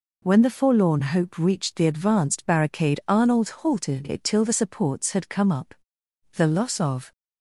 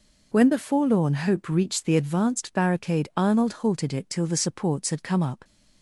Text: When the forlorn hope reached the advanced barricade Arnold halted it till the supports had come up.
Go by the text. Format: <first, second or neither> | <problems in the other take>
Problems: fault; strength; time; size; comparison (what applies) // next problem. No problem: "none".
second | goes on to say "The loss of"; noticeable; from 6.3 s on; 0.76 s long